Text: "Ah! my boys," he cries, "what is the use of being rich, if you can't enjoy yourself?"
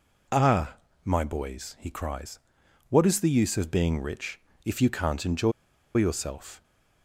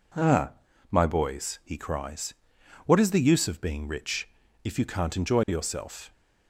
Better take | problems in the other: second | pauses between "enjoy" and "yourself"; at 5.5 s; 0.44 s long

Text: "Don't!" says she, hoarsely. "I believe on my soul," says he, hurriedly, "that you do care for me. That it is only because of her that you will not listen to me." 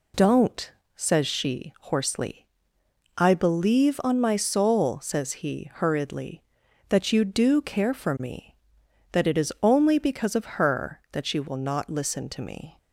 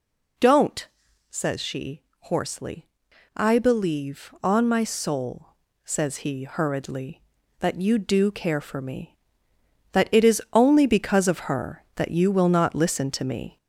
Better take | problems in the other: first | gets louder; throughout; 4 dB

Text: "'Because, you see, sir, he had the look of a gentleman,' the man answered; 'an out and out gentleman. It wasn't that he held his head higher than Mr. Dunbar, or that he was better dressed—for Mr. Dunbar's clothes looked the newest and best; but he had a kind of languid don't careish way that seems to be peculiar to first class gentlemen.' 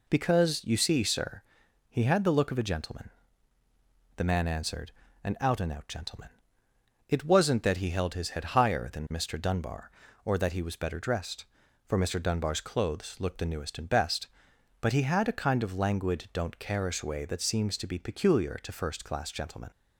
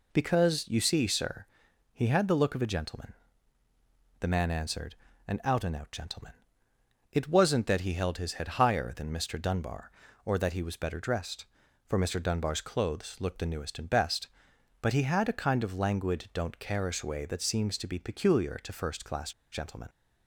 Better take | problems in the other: first | pauses between "class" and "gentlemen"; slight; at 19.3 s; 0.21 s long

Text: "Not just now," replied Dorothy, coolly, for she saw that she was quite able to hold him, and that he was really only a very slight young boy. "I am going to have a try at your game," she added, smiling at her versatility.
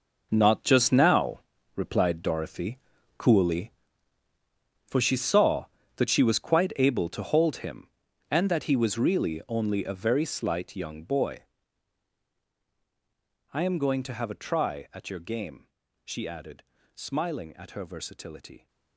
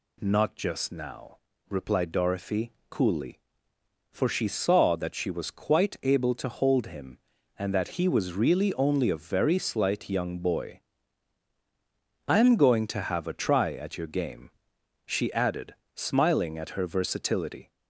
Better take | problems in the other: second | gets quieter; strong; throughout; 13 dB

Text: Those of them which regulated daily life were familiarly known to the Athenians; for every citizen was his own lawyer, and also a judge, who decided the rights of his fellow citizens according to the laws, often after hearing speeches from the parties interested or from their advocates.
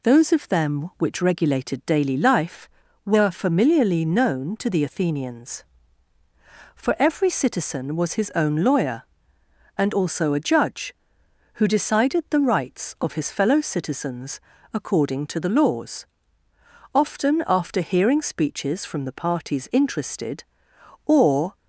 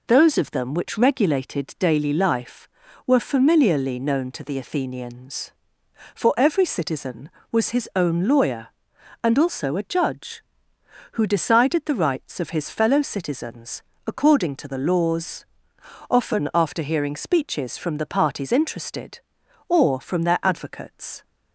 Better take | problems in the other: second | pauses between "citizens" and "according"; slight; at 14.3 s; 0.34 s long; slight in the second // stops before "from their advocates"; at 21.5 s

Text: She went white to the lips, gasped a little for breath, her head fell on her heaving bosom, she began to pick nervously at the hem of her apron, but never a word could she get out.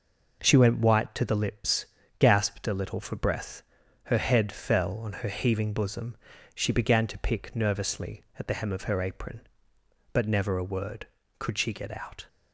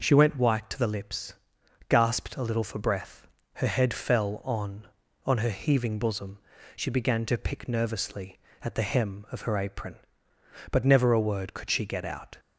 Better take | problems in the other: first | says "on" twice; at 5.2 s

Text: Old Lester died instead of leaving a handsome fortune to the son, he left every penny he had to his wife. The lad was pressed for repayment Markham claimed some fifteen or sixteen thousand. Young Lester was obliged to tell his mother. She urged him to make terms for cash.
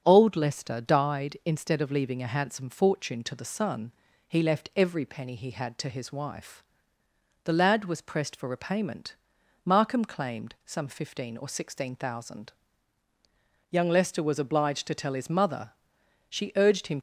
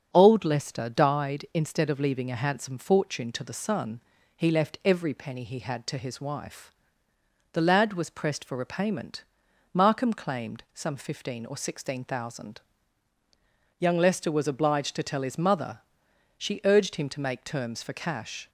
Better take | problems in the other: second | starts louder than the rest; until 1.0 s; 7 dB; also in the second // pauses between "repayment" and "Markham"; noticeable; at 9.1 s; 0.50 s long; noticeable in the second // stops before "to make terms for cash"; at 16.9 s

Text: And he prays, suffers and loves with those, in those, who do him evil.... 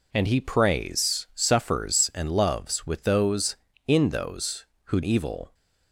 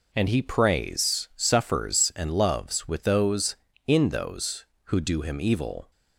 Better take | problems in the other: second | skips "do him"; at 5.0 s

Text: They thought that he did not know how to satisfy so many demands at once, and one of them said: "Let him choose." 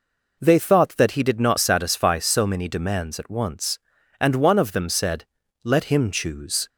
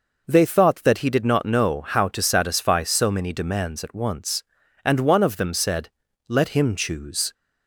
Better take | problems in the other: second | skips "know how to"; at 1.5 s

